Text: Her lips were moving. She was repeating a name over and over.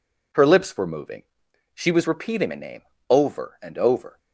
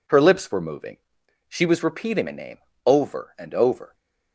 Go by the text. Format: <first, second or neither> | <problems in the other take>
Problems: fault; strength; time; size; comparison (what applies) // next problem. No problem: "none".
neither | pauses between "name" and "over"; slight; the same in both